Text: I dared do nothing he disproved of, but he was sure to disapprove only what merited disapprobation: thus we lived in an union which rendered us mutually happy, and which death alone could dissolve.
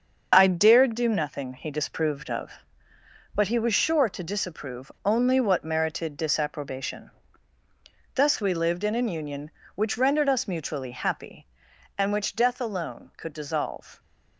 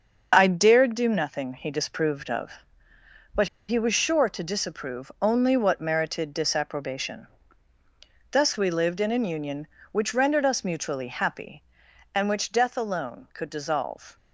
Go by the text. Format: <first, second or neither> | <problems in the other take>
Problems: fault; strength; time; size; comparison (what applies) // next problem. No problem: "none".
first | starts louder than the rest; until 1.3 s; 6 dB; also in the first // pauses between "but" and "he"; slight; at 3.4 s; 0.22 s long